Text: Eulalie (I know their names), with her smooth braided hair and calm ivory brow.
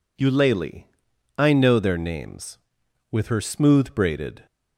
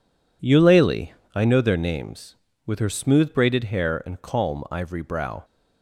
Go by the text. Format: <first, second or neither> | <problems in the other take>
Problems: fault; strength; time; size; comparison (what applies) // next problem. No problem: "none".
second | stops before "hair and calm ivory brow"; at 4.4 s